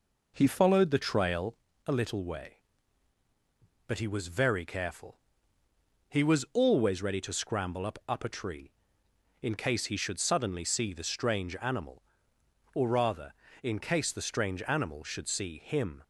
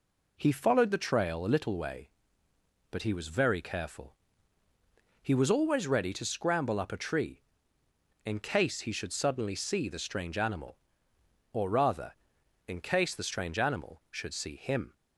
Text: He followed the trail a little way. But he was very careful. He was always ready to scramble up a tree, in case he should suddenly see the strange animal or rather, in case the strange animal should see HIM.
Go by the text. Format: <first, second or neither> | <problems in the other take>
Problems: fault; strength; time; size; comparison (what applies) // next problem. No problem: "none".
second | pauses between "trail" and "a"; slight; at 1.5 s; 0.32 s long // says "up" twice; at 8.0 s